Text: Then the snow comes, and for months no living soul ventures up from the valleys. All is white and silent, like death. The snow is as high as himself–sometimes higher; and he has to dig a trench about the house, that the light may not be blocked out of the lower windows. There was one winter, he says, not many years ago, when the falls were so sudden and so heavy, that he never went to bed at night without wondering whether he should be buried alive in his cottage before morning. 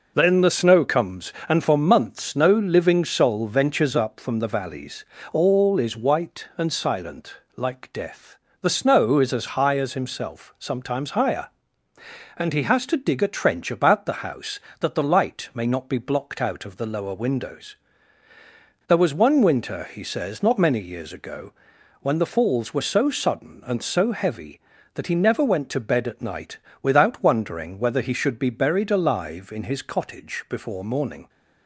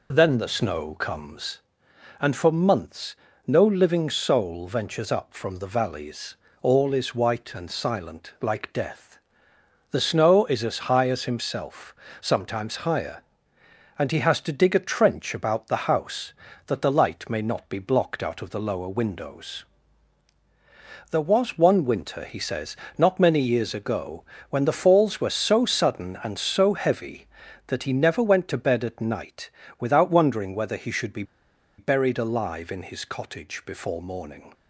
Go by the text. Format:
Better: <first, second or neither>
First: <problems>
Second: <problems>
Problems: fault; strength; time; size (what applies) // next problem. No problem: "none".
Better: first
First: pauses between "night" and "without"; slight; at 26.5 s; 0.24 s long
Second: pauses between "months" and "no"; slight; at 3.1 s; 0.32 s long // pauses between "night" and "without"; slight; at 29.4 s; 0.30 s long // pauses between "be" and "buried"; noticeable; at 31.2 s; 0.55 s long